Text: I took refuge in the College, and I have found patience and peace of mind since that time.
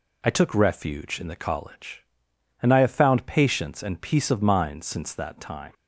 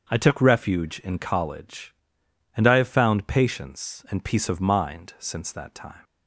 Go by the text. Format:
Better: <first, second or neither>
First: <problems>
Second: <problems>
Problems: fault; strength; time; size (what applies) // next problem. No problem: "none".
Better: first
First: none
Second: starts louder than the rest; until 1.1 s; 6.5 dB // skips "the"; at 1.1 s